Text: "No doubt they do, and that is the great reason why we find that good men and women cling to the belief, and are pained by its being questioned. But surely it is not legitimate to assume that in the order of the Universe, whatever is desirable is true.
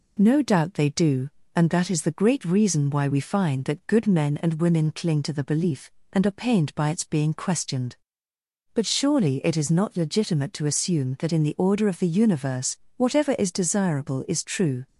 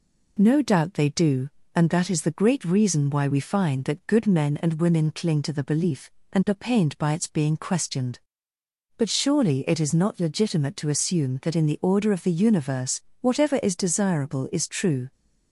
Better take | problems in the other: neither | none

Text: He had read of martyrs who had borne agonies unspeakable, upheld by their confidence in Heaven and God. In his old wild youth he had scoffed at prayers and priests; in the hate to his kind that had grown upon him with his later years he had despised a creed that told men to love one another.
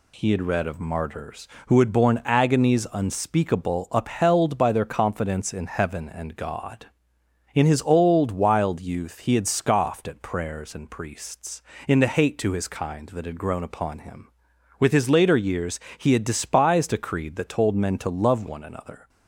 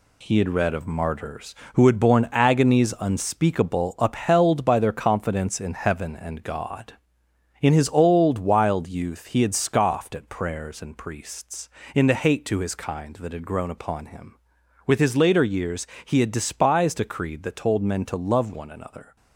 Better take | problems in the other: first | gets quieter; throughout; 7 dB // pauses between "years" and "he"; slight; at 15.8 s; 0.18 s long; slight in the first

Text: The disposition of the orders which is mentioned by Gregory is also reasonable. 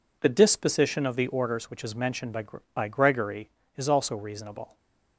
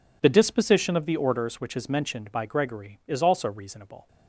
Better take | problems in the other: second | says "by" twice; at 2.7 s // stays silent after the last word; slight; from 4.6 s on; 0.5 s long

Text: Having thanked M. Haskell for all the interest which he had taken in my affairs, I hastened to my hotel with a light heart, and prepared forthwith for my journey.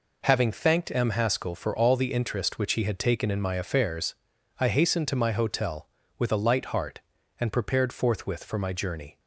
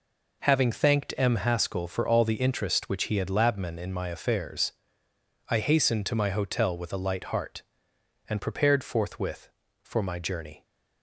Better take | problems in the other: first | says "labmen" for "taken"; at 3.2 s

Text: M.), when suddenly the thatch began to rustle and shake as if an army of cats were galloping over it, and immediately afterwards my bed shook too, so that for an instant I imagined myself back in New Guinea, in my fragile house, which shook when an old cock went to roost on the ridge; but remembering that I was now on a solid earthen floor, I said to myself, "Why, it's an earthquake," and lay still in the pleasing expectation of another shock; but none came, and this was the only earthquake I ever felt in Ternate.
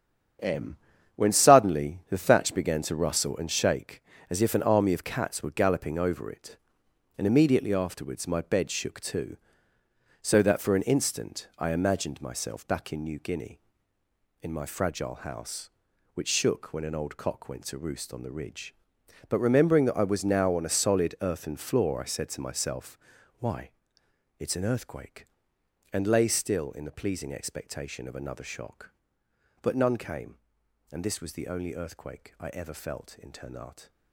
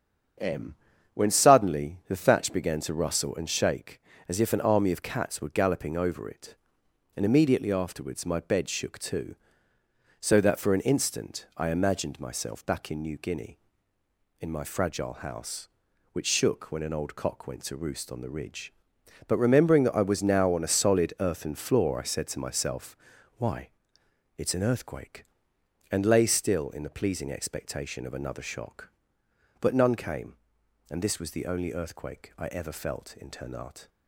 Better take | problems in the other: second | gets quieter; strong; throughout; 9 dB // starts louder than the rest; strong; until 1.8 s; 8.5 dB; strong in the second

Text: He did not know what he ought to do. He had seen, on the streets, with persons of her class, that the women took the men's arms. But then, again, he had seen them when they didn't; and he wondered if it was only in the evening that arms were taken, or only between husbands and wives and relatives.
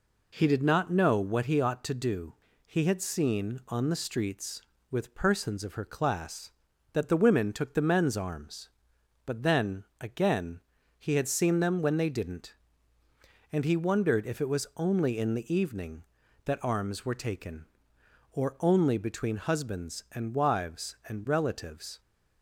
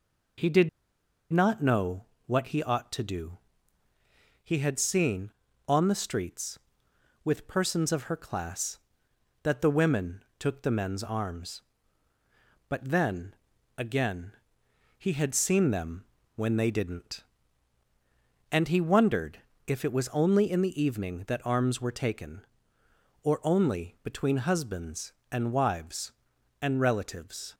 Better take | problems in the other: first | pauses between "did" and "not"; noticeable; at 0.6 s; 0.62 s long // pauses between "know" and "what"; slight; at 2.0 s; 0.22 s long // pauses between "women" and "took"; slight; at 10.2 s; 0.18 s long // pauses between "them" and "when"; slight; at 16.0 s; 0.32 s long // pauses between "wondered" and "if"; slight; at 19.3 s; 0.28 s long

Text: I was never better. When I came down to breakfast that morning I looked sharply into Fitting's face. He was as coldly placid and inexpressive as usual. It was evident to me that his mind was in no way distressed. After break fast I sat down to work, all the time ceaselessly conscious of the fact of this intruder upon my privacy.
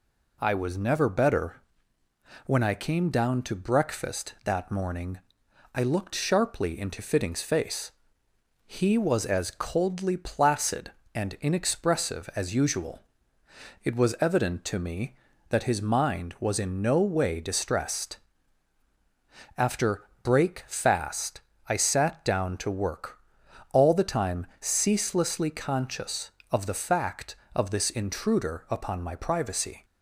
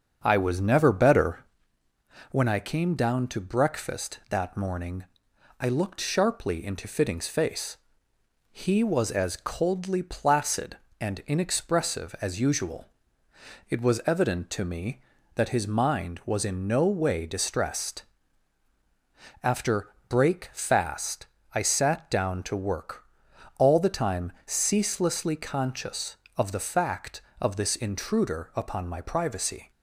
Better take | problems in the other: first | starts louder than the rest; until 1.6 s; 6.5 dB // pauses between "morning" and "I"; noticeable; at 5.0 s; 0.56 s long; noticeable in the first // pauses between "After" and "break"; slight; at 19.9 s; 0.18 s long; slight in the first // pauses between "fast" and "I"; slight; at 21.2 s; 0.28 s long; slight in the first

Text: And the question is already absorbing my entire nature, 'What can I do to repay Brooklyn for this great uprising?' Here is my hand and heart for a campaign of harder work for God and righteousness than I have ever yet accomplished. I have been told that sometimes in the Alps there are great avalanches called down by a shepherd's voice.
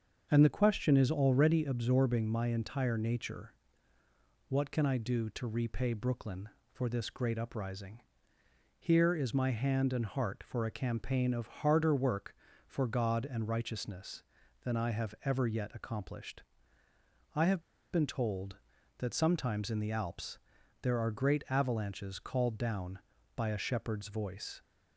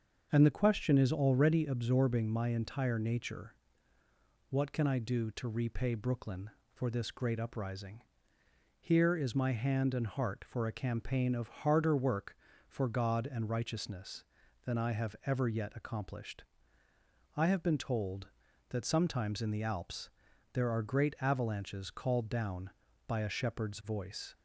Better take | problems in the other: second | starts louder than the rest; until 1.3 s; 6.5 dB; also in the second // pauses between "have" and "been"; slight; at 17.6 s; 0.31 s long // pauses between "Alps" and "there"; at 20.3 s; 0.44 s long; also in the second

